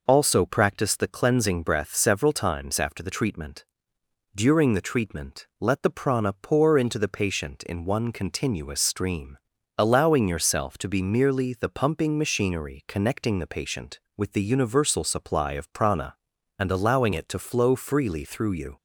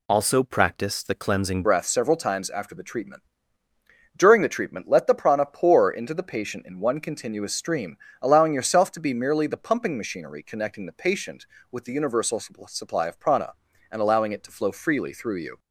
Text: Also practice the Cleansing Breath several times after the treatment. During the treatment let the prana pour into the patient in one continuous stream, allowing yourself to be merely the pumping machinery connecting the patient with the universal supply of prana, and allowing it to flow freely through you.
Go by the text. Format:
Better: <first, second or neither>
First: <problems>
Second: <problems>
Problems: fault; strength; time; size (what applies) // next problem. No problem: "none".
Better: first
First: none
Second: changes voice at "Breath"; from 1.6 s on; 13.9 s long